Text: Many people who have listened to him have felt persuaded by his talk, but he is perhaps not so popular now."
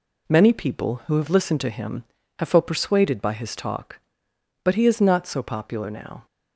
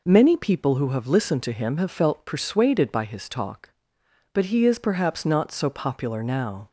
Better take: second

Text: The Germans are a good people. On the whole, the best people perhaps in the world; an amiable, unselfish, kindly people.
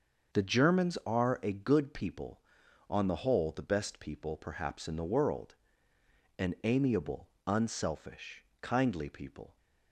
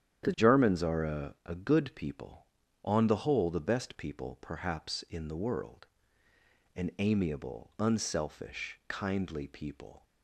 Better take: first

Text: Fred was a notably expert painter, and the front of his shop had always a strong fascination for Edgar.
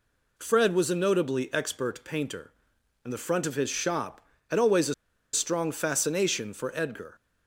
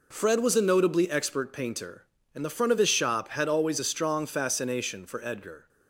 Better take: second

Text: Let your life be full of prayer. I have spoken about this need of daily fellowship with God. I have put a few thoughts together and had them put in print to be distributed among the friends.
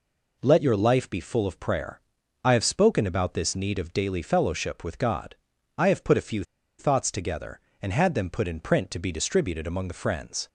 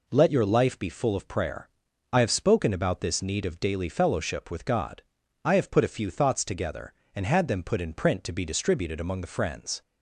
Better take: second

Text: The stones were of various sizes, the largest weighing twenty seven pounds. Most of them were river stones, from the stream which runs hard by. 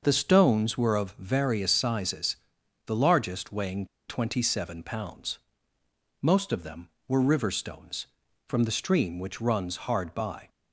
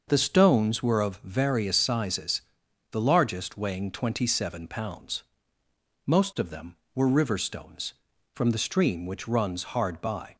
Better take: second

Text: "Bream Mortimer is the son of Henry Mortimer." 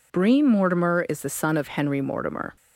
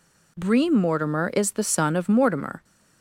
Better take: first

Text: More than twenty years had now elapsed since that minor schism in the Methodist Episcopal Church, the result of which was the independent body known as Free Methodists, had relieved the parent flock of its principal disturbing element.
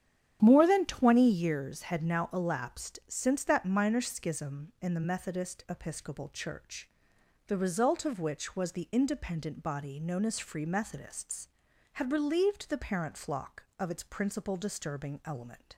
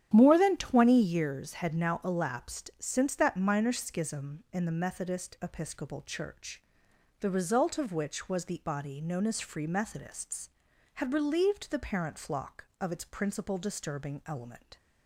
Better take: first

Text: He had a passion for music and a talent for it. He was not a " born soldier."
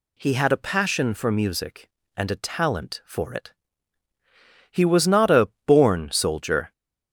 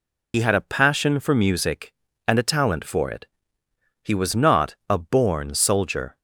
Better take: first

